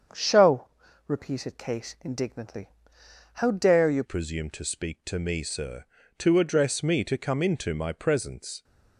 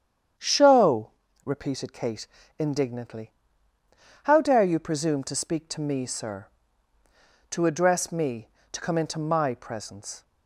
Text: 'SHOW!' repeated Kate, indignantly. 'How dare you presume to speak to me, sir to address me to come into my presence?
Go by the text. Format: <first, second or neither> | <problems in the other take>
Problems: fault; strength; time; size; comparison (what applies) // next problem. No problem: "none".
second | starts louder than the rest; strong; until 1.5 s; 7.5 dB; strong in the second // changes voice at "presume"; from 4.0 s on; 4.6 s long